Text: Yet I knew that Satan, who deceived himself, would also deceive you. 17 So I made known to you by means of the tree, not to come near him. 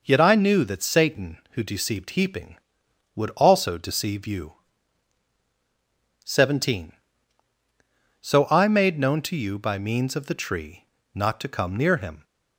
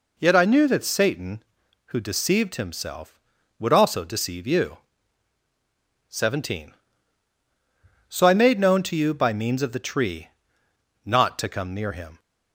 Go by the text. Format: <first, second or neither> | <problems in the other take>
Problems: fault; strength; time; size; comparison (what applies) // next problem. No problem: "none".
second | says "heaping" for "himself"; at 2.1 s